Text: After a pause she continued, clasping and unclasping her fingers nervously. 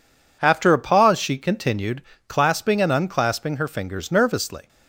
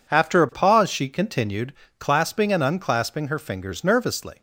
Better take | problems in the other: neither | none

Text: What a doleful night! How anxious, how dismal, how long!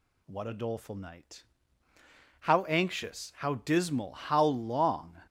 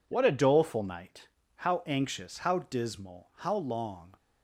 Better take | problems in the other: neither | none

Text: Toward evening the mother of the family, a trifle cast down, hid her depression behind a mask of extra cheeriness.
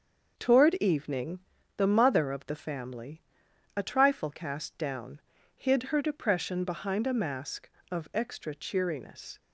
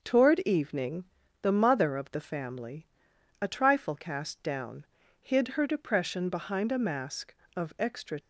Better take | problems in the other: first | starts louder than the rest; until 1.0 s; 6 dB; also in the first // pauses between "evening" and "the"; at 1.0 s; 0.38 s long; also in the first // stops before "cheeriness"; at 8.1 s

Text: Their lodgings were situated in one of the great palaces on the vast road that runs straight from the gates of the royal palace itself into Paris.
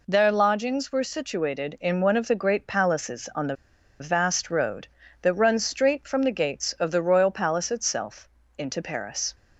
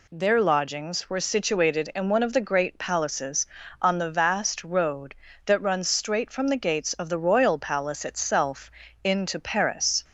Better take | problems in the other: second | pauses between "the" and "vast"; at 3.5 s; 0.45 s long // pauses between "itself" and "into"; slight; at 8.2 s; 0.30 s long; slight in the second

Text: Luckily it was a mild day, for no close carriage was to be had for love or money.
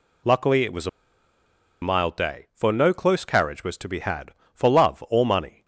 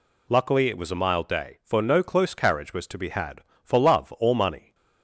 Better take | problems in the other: second | pauses between "a" and "mild"; noticeable; at 0.8 s; 0.93 s long

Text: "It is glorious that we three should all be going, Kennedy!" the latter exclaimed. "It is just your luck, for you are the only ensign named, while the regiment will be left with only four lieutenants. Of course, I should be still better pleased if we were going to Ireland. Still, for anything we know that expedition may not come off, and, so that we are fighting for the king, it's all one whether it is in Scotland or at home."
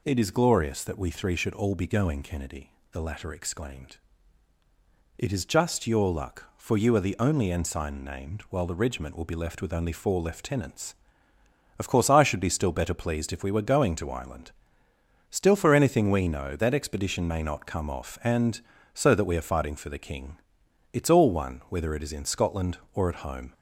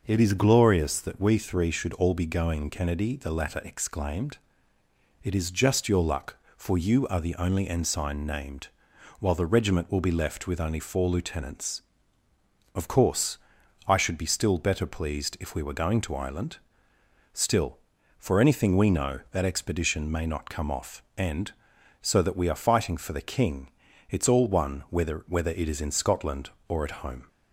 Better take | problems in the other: first | says "whether" twice; at 25.2 s

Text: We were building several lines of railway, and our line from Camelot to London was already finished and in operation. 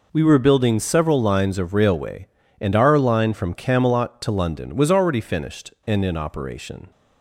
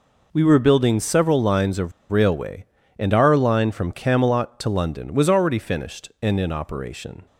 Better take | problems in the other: first | pauses between "of" and "railway"; slight; at 1.9 s; 0.17 s long

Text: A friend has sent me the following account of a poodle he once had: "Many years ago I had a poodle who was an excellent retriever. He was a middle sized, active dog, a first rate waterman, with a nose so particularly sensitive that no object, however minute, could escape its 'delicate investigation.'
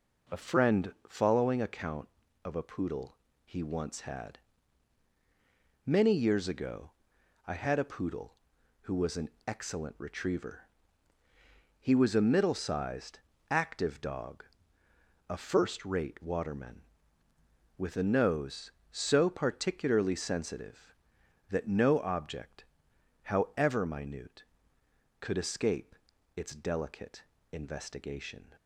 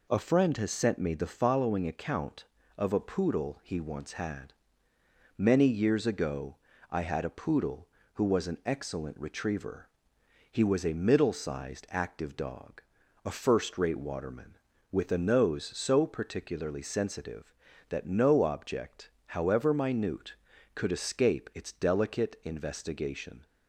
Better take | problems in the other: second | skips "has sent me the"; at 0.9 s // pauses between "poodle" and "he"; slight; at 3.1 s; 0.30 s long // pauses between "ago" and "I"; noticeable; at 6.9 s; 0.54 s long; slight in the second // pauses between "an" and "excellent"; slight; at 9.2 s; 0.16 s long // pauses between "escape" and "its"; at 25.9 s; 0.40 s long // pauses between "delicate" and "investigation"; slight; at 27.2 s; 0.32 s long

